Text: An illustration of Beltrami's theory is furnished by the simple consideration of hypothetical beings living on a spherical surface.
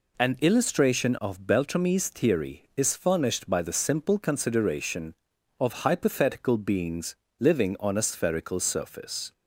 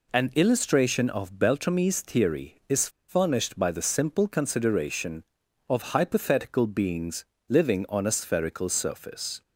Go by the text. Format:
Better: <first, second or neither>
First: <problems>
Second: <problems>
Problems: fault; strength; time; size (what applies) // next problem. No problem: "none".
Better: first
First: pauses between "beings" and "living"; slight; at 7.1 s; 0.22 s long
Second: pauses between "is" and "furnished"; slight; at 2.8 s; 0.20 s long // pauses between "beings" and "living"; slight; at 7.2 s; 0.22 s long